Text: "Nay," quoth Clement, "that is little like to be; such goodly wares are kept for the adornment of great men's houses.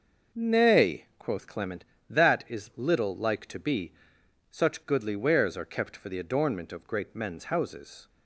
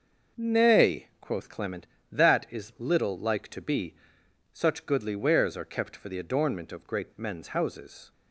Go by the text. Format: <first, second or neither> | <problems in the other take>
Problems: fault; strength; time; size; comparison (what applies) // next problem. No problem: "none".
neither | none